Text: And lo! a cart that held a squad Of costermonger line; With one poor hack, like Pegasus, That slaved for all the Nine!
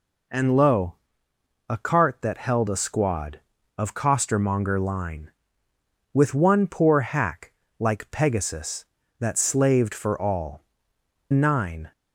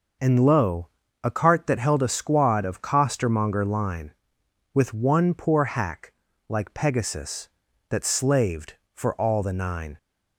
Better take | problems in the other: second | skips "the"; at 10.9 s

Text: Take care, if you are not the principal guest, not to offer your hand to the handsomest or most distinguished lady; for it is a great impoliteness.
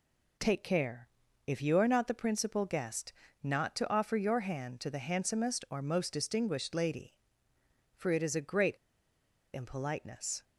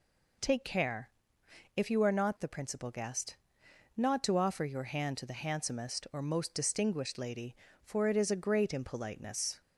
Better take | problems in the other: second | pauses between "great" and "impoliteness"; noticeable; at 8.7 s; 0.78 s long

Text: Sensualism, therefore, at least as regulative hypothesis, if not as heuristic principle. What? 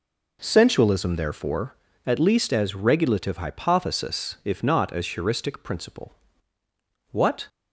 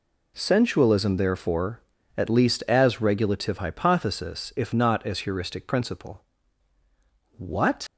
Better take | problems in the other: first | leaves "What" unfinished; at 7.8 s; 80 ms

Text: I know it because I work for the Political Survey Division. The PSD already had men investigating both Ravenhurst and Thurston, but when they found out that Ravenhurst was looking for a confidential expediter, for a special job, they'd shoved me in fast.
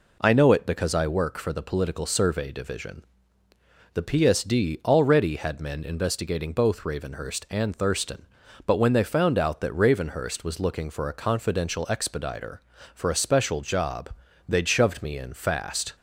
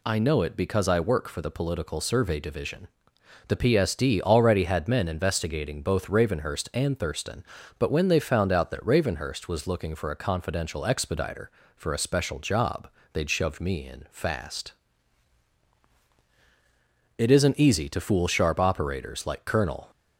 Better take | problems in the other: first | goes on to say "It isn't easy to fool sharp operators like Colonel"; strong; from 17.1 s on; 2.7 s long

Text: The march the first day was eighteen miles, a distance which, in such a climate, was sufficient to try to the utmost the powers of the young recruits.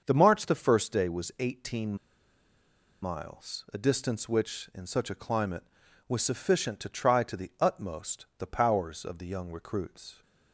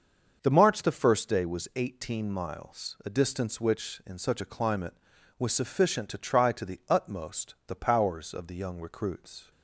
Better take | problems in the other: second | starts louder than the rest; until 1.0 s; 6.5 dB; also in the second // pauses between "eighteen" and "miles"; at 1.9 s; 1.0 s long

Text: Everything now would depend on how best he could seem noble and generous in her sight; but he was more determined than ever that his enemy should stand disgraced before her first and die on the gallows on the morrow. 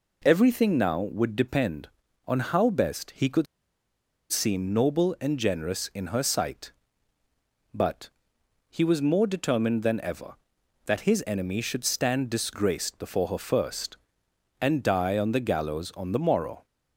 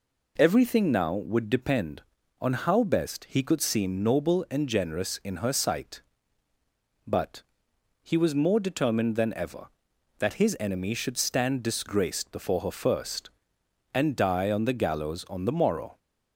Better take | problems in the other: second | pauses between "could" and "seem"; noticeable; at 3.4 s; 0.86 s long // pauses between "but" and "he"; noticeable; at 8.0 s; 0.60 s long; noticeable in the second

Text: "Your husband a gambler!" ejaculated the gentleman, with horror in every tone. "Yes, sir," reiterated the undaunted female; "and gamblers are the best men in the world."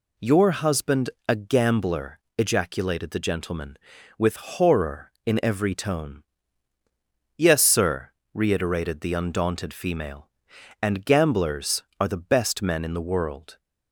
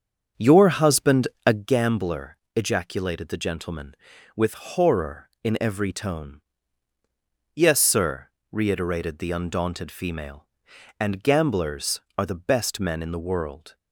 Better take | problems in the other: first | starts louder than the rest; strong; until 1.7 s; 7 dB // pauses between "husband" and "a"; slight; at 1.2 s; 0.18 s long; slight in the first

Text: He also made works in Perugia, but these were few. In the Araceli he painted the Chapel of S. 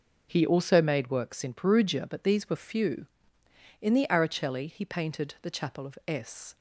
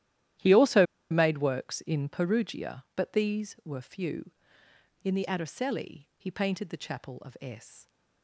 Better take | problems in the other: first | starts louder than the rest; strong; until 1.6 s; 12.5 dB // pauses between "also" and "made"; slight; at 0.8 s; 0.25 s long

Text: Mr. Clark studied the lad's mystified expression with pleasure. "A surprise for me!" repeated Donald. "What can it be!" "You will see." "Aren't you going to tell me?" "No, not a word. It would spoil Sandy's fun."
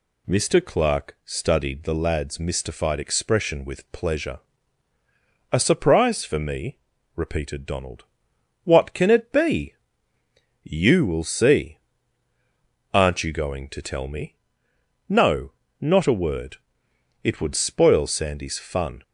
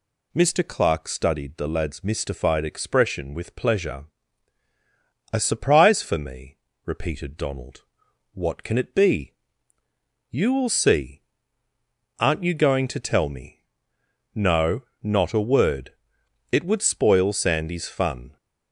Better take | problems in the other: neither | none

